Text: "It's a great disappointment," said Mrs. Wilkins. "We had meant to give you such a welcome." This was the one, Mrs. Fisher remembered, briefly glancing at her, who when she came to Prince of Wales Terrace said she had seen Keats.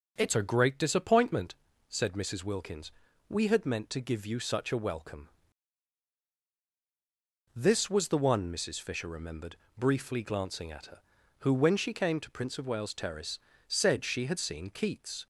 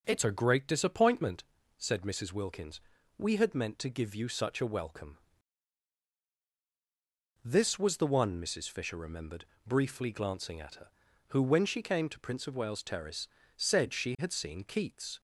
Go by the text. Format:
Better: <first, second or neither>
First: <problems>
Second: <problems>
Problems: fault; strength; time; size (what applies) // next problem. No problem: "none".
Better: neither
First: pauses between "Terrace" and "said"; slight; at 13.3 s; 0.30 s long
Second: pauses between "Terrace" and "said"; slight; at 13.2 s; 0.30 s long